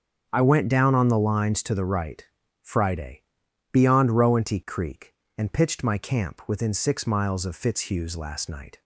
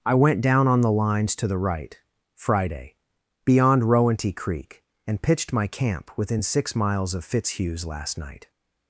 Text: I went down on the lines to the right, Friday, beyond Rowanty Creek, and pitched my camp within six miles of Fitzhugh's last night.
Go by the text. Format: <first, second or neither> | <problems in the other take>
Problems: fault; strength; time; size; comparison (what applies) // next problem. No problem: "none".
neither | starts louder than the rest; the same in both